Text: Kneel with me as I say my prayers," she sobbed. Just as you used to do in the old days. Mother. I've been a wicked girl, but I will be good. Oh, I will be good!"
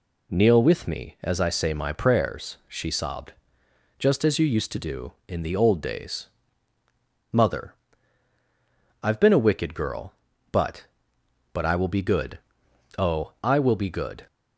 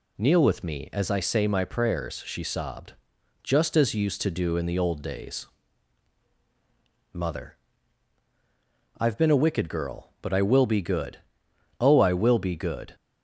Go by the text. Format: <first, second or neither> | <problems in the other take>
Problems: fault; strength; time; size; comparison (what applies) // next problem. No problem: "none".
second | says "but" twice; at 11.5 s